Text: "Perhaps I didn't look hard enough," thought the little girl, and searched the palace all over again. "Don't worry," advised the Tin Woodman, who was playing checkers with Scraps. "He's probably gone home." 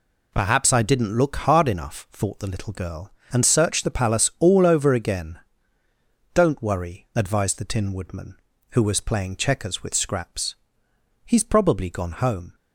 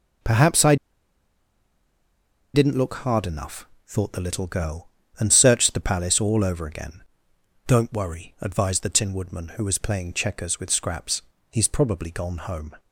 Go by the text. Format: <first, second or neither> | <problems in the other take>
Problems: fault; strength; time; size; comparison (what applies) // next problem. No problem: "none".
first | pauses between "I" and "didn't"; strong; at 0.7 s; 1.7 s long